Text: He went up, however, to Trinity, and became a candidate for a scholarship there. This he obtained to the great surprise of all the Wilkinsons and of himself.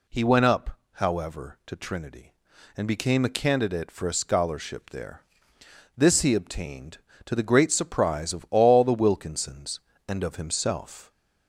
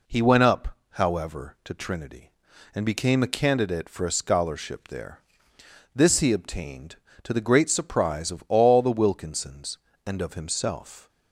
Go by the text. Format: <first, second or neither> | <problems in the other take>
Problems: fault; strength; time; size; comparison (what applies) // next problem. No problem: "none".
second | gets louder; slight; throughout; 2.5 dB